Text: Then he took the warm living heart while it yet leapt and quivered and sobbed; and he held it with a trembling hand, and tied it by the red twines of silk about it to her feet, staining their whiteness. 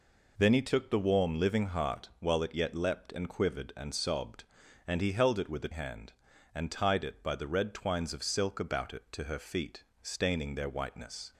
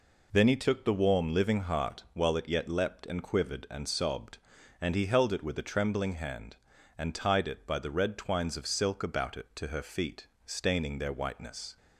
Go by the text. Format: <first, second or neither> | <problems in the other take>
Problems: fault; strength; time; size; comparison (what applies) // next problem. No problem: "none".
second | skips "trembling"; at 5.7 s